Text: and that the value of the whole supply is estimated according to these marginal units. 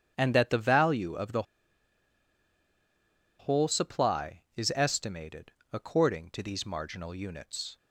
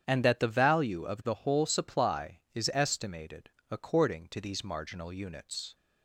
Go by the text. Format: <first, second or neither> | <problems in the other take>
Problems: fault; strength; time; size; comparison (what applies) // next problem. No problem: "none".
second | starts louder than the rest; strong; until 1.1 s; 8.5 dB; strong in the second // pauses between "the" and "whole"; strong; at 1.4 s; 1.9 s long // pauses between "estimated" and "according"; slight; at 5.5 s; 0.22 s long; slight in the second